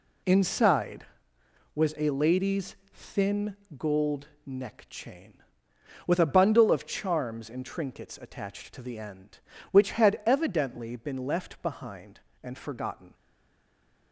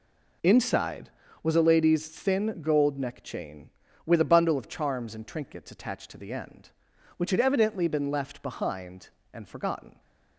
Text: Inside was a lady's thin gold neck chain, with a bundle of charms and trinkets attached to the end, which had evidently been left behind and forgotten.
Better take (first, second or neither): second